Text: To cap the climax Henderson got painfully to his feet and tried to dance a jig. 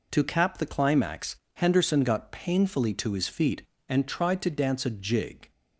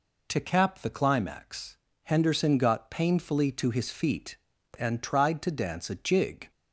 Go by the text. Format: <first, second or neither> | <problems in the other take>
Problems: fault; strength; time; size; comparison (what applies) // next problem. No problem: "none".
neither | pauses between "climax" and "Henderson"; slight; the same in both